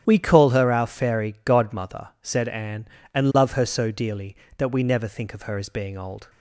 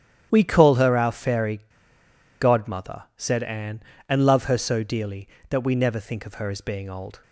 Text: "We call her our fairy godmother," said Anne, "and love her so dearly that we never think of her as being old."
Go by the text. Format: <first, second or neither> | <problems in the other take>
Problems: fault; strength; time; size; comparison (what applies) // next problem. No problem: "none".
first | starts louder than the rest; strong; until 1.3 s; 10 dB; strong in the first // pauses between "fairy" and "godmother"; noticeable; at 1.6 s; 0.78 s long